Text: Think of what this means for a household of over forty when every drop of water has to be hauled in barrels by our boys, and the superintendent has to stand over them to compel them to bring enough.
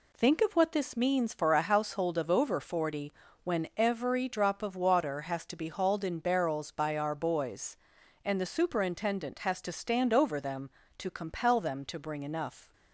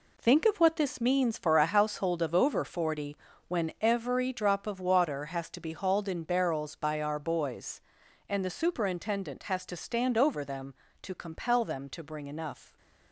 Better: first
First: pauses between "forty" and "when"; slight; at 3.1 s; 0.32 s long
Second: gets quieter; strong; throughout; 8.5 dB // pauses between "forty" and "when"; slight; at 3.1 s; 0.32 s long

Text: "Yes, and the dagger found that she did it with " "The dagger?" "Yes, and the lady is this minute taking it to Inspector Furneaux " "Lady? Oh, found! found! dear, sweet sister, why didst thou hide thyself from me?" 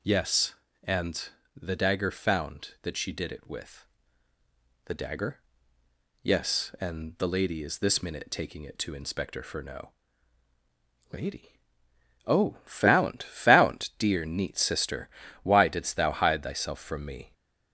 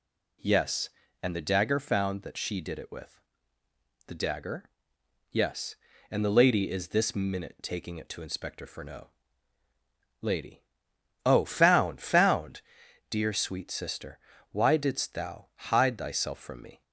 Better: second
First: pauses between "and" and "the"; slight; at 1.2 s; 0.28 s long // says "neat" for "sweet"; at 14.2 s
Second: none

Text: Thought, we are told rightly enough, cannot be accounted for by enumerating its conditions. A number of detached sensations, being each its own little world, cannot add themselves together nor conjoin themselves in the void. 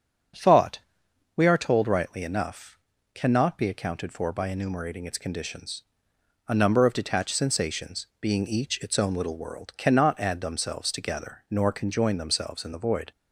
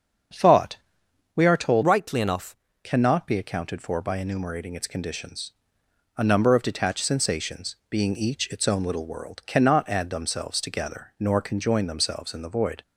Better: first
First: starts louder than the rest; strong; until 1.9 s; 7 dB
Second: starts louder than the rest; strong; until 1.9 s; 7.5 dB // changes voice from "rightly" to "enough"; from 1.8 to 2.5 s; 0.7 s long

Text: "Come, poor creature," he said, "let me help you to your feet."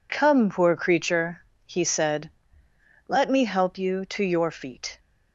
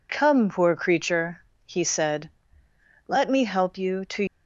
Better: first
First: none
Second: stops before "your feet"; at 4.2 s

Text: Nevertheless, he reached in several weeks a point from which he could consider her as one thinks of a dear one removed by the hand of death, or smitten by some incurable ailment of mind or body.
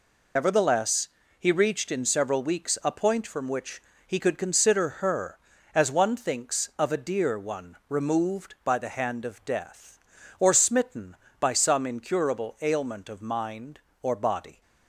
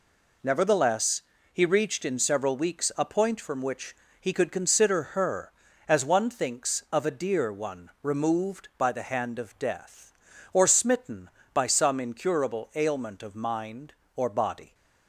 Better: second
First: loses the start of "Nevertheless"; at 0.3 s; 70 ms // pauses between "which" and "he"; slight; at 3.8 s; 0.26 s long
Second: pauses between "which" and "he"; slight; at 3.9 s; 0.26 s long

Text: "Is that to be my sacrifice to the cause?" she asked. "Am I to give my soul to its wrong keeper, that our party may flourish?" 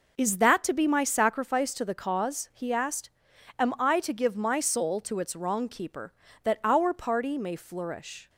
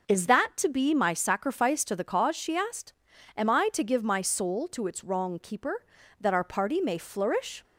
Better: second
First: says "he" for "she"; at 2.5 s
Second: none

